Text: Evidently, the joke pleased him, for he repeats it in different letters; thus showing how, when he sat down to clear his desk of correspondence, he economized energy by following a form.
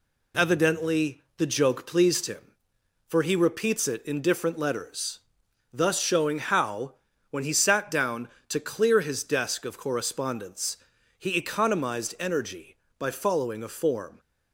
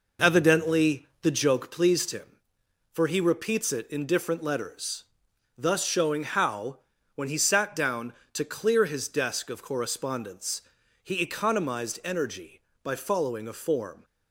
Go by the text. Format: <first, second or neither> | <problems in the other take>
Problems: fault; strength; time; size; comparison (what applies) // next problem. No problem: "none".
first | starts louder than the rest; noticeable; until 1.6 s; 4.5 dB